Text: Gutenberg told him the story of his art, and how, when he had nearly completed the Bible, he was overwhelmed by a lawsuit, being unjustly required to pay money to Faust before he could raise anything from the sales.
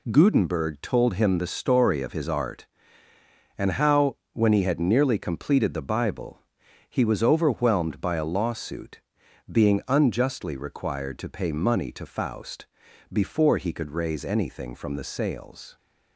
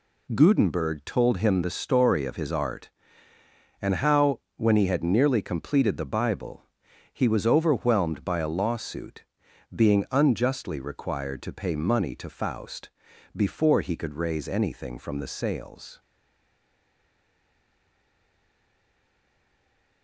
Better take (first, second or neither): first